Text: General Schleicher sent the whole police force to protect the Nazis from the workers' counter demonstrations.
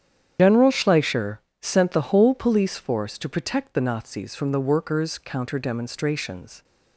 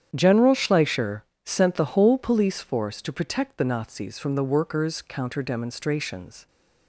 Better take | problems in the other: second | loses the start of "General"; at 0.3 s; 105 ms // starts louder than the rest; strong; until 1.6 s; 9 dB; strong in the second // pauses between "Schleicher" and "sent"; slight; at 1.3 s; 0.24 s long; slight in the second

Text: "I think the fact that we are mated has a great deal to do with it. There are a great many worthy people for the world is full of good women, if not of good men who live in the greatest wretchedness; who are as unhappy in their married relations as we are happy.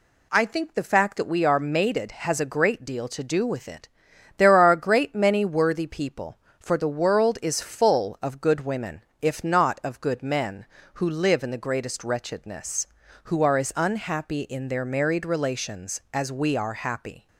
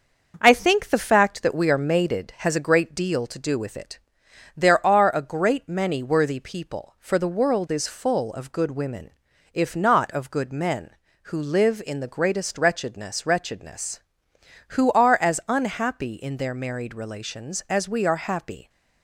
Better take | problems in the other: first | starts louder than the rest; noticeable; until 1.4 s; 6 dB // says "wretchedness" twice; at 13.2 s

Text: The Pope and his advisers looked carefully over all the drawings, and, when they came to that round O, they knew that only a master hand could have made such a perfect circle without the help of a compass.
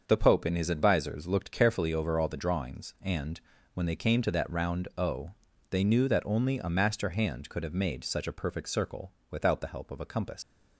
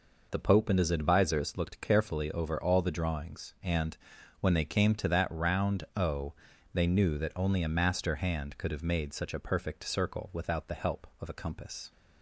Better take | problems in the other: second | starts louder than the rest; until 1.0 s; 6.5 dB // pauses between "circle" and "without"; slight; at 9.1 s; 0.20 s long // leaves "compass" unfinished; at 10.4 s; 110 ms

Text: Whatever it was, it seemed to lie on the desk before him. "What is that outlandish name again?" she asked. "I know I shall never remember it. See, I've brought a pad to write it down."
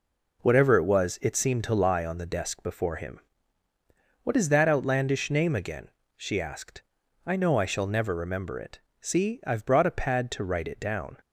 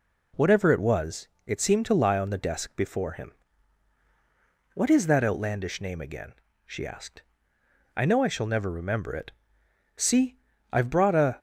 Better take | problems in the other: first | stops before "pad to write it down"; at 11.3 s

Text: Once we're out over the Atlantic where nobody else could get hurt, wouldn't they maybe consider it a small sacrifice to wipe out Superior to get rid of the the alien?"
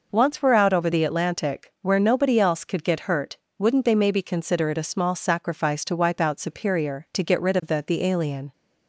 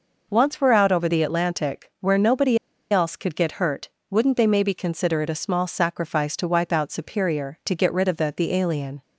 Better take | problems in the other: first | pauses between "nobody" and "else"; slight; at 2.5 s; 0.33 s long

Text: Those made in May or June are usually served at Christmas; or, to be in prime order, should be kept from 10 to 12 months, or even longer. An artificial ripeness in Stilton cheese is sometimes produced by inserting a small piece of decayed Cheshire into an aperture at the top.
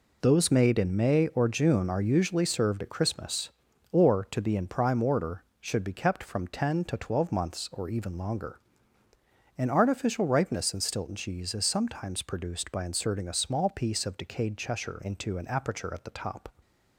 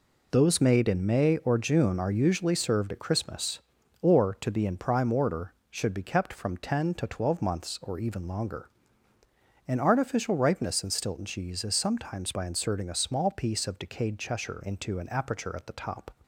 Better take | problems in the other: first | skips "produced"; at 12.3 s

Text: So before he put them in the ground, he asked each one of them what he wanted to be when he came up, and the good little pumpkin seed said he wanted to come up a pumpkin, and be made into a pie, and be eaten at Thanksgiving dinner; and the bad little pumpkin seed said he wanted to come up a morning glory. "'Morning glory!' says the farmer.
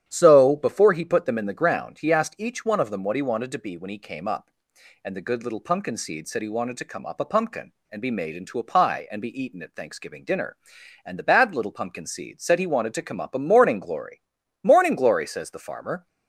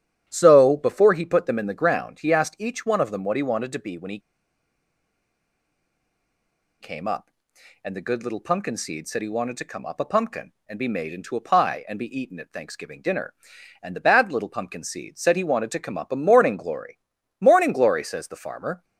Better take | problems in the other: first | starts louder than the rest; strong; until 1.2 s; 9.5 dB; strong in the first // pauses between "he" and "came"; strong; at 4.1 s; 2.6 s long

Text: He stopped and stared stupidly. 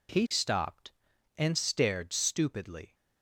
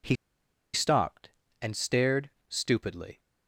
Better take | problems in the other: first | pauses between "He" and "stopped"; noticeable; at 0.1 s; 0.58 s long // pauses between "stared" and "stupidly"; slight; at 2.3 s; 0.18 s long

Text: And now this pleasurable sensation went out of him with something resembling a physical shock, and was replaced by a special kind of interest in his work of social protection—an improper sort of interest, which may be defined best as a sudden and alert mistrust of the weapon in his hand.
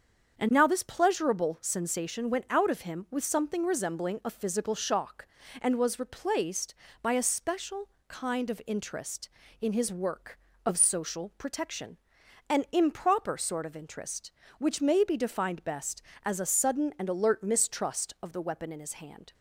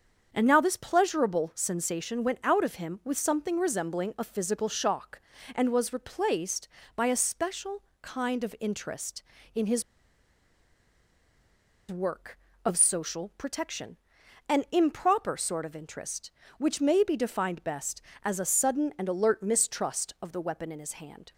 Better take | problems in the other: first | starts louder than the rest; strong; until 1.3 s; 7 dB; also in the first // pauses between "special" and "kind"; slight; at 7.8 s; 0.20 s long; slight in the first // pauses between "his" and "work"; strong; at 9.8 s; 2.0 s long

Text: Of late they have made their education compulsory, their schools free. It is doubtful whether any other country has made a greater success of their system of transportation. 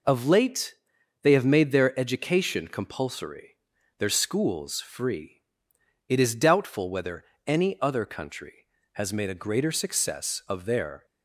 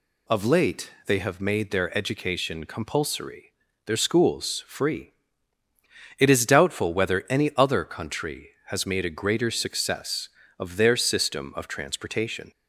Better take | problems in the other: second | pauses between "late" and "they"; noticeable; at 0.7 s; 0.48 s long // pauses between "whether" and "any"; slight; at 7.2 s; 0.22 s long // stops before "system of transportation"; at 11.0 s

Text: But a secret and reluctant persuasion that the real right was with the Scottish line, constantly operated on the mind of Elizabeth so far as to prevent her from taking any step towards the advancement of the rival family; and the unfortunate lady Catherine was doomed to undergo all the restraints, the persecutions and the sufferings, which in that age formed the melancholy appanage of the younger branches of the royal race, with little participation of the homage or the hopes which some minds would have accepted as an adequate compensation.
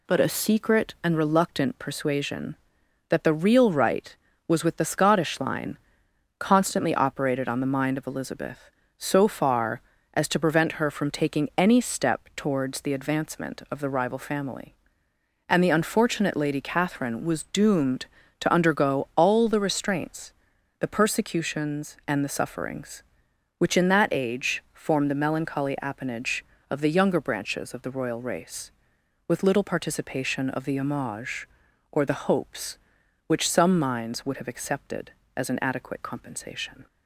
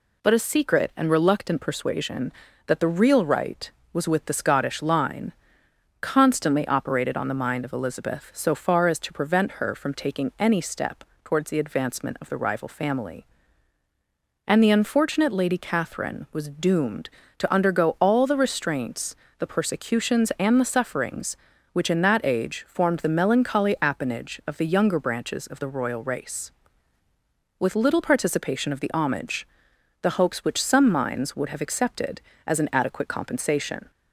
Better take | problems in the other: first | pauses between "step" and "towards"; slight; at 11.0 s; 0.20 s long // skips "or"; at 29.7 s

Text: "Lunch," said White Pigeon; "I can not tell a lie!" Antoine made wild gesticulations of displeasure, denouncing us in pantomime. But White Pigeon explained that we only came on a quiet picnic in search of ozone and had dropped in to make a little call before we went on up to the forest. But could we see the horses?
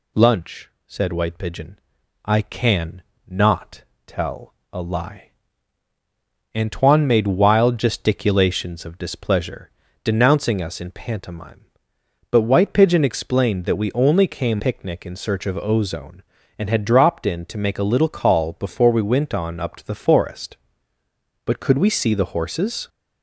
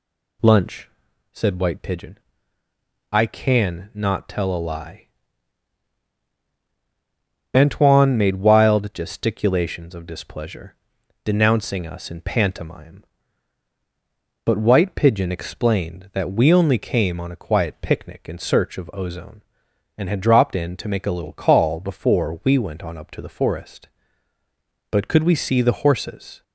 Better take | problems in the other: second | pauses between "can" and "not"; slight; at 3.0 s; 0.24 s long // pauses between "not" and "tell"; slight; at 3.8 s; 0.24 s long // pauses between "tell" and "a"; slight; at 4.5 s; 0.18 s long // skips "on a quiet"; at 14.5 s

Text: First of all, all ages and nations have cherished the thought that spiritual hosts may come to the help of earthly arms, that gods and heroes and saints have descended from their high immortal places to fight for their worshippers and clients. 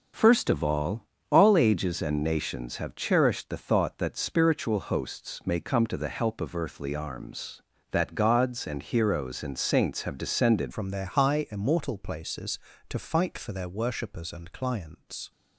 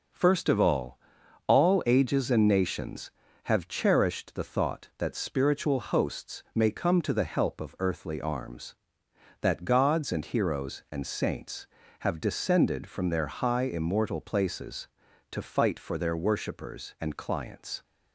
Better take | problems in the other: second | changes voice at "from"; from 10.7 s on; 4.6 s long

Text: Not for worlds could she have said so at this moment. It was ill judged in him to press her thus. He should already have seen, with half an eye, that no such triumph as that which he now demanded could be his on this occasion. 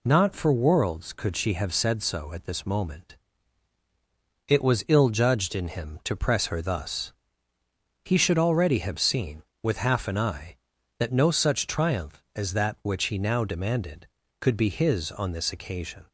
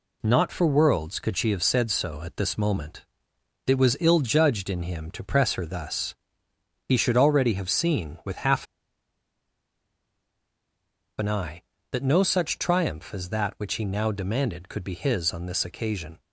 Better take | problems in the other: first | pauses between "half" and "an"; strong; at 8.6 s; 2.5 s long

